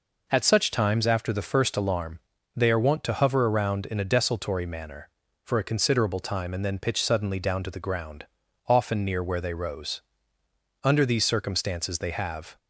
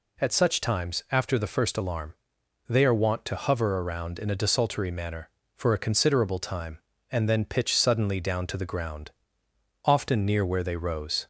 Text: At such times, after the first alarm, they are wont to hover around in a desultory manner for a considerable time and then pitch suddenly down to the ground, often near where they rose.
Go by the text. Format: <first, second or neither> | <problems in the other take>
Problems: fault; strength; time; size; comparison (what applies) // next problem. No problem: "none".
second | goes on to say "Under these circumstances they have"; strong; from 10.8 s on; 1.7 s long